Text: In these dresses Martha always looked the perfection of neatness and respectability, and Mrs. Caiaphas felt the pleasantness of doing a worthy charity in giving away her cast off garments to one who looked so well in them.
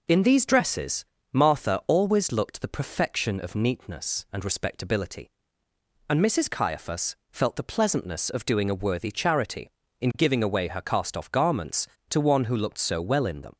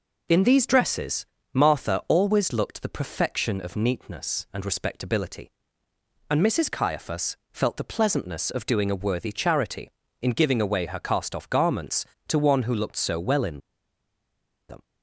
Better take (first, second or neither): first